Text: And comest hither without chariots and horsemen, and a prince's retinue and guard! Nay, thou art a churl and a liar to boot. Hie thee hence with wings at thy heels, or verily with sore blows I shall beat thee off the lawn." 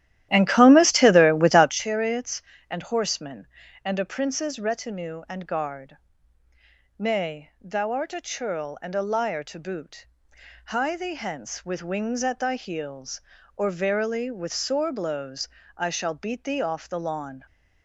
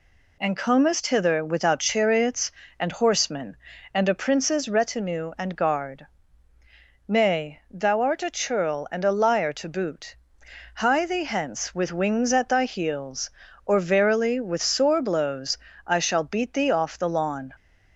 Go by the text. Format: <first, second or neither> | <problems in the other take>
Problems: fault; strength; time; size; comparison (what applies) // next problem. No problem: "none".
second | starts louder than the rest; strong; until 1.8 s; 13 dB // pauses between "blows" and "I"; slight; at 15.4 s; 0.28 s long; slight in the second